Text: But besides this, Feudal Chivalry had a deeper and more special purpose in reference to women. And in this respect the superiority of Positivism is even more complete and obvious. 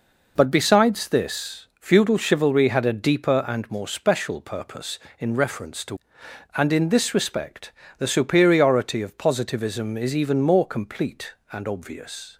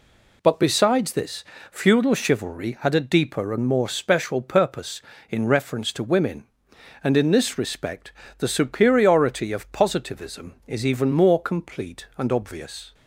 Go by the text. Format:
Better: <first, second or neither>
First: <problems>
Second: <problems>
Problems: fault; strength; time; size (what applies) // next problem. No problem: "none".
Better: second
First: skips "women"; at 6.2 s // pauses between "respect" and "the"; slight; at 7.7 s; 0.26 s long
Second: pauses between "respect" and "the"; slight; at 8.1 s; 0.26 s long